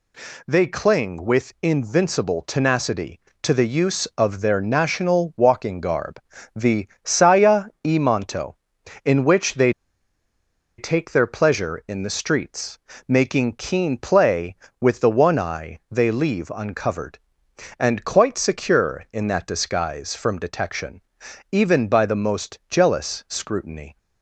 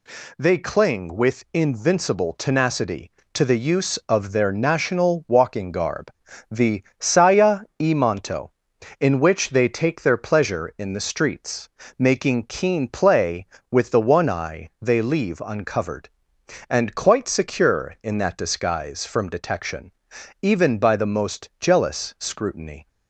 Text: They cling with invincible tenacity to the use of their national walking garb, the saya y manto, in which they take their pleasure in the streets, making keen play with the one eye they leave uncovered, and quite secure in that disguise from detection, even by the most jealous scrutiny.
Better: second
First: pauses between "the" and "saya"; slight; at 6.8 s; 0.16 s long // pauses between "saya" and "y"; slight; at 7.6 s; 0.18 s long // pauses between "they" and "take"; at 9.7 s; 1.0 s long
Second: pauses between "the" and "saya"; slight; at 6.8 s; 0.16 s long // pauses between "saya" and "y"; slight; at 7.5 s; 0.18 s long

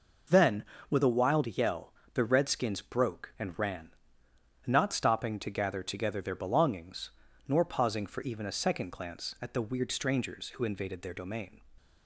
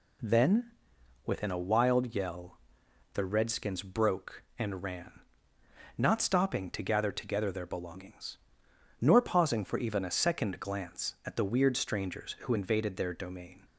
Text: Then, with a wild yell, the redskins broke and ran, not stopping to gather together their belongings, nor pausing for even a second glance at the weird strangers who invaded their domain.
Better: first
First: none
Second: says "within" for "with"; at 1.2 s

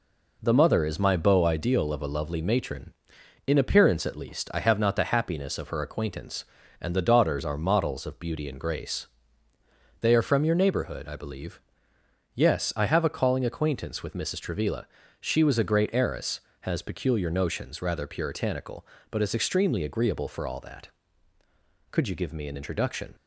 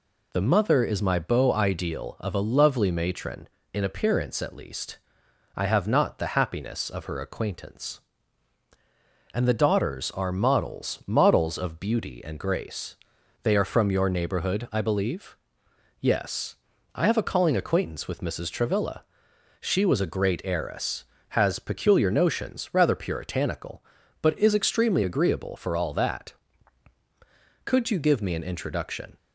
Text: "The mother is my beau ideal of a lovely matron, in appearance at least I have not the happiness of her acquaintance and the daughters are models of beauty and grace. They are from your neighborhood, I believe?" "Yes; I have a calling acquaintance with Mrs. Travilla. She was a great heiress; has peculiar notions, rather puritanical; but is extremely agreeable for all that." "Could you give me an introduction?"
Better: first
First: none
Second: pauses between "least" and "I"; noticeable; at 4.9 s; 0.58 s long // says "models" twice; at 11.0 s

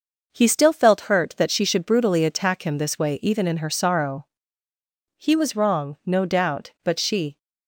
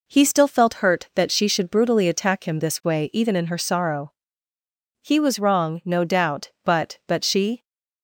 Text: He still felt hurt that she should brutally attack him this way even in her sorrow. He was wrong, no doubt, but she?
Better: first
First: none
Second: says "but" twice; at 7.0 s

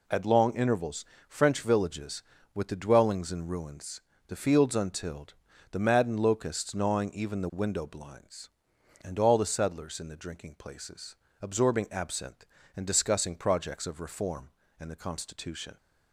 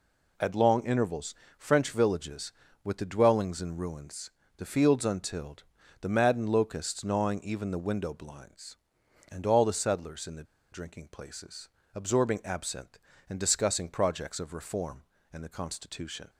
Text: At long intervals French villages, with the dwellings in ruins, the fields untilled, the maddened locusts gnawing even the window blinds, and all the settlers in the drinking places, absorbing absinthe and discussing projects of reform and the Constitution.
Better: first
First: pauses between "intervals" and "French"; slight; at 1.0 s; 0.24 s long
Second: pauses between "intervals" and "French"; slight; at 1.3 s; 0.24 s long // pauses between "the" and "drinking"; slight; at 10.4 s; 0.28 s long

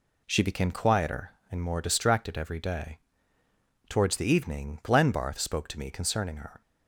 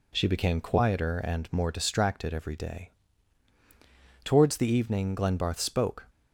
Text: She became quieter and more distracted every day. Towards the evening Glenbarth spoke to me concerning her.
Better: first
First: none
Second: stops before "to me concerning her"; at 6.0 s

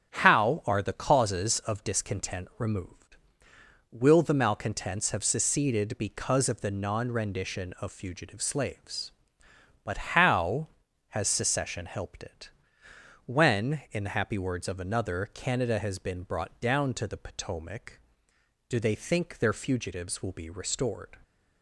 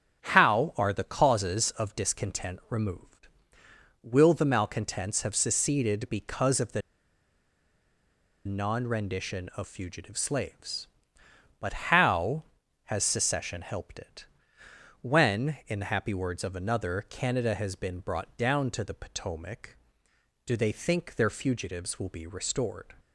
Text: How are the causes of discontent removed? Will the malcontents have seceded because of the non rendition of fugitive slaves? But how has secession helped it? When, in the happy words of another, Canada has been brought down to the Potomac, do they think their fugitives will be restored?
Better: first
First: starts louder than the rest; strong; until 1.1 s; 8.5 dB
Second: starts louder than the rest; strong; until 1.2 s; 8 dB // pauses between "the" and "non"; strong; at 6.8 s; 1.6 s long

